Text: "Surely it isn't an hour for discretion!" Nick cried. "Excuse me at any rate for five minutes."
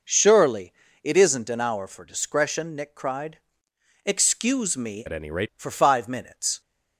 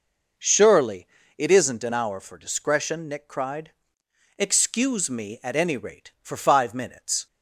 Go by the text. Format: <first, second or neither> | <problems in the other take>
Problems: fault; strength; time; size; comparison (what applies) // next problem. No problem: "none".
second | pauses between "Surely" and "it"; slight; at 0.7 s; 0.32 s long; slight in the second // changes voice from "at" to "rate"; from 5.0 to 5.4 s; 0.4 s long